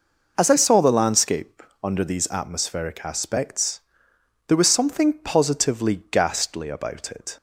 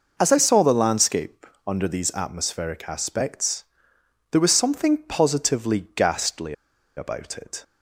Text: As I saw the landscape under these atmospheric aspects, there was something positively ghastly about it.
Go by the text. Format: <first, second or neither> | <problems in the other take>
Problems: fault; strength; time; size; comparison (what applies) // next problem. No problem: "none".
first | pauses between "landscape" and "under"; slight; at 1.4 s; 0.22 s long; slight in the first // pauses between "ghastly" and "about"; at 6.5 s; 0.43 s long